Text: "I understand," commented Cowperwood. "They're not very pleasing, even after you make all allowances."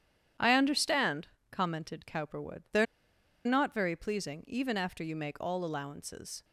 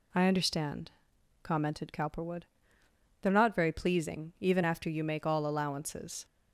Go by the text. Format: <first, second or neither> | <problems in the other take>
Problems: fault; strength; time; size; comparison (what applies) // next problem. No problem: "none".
second | starts louder than the rest; strong; until 1.6 s; 10 dB // pauses between "They're" and "not"; noticeable; at 2.8 s; 0.60 s long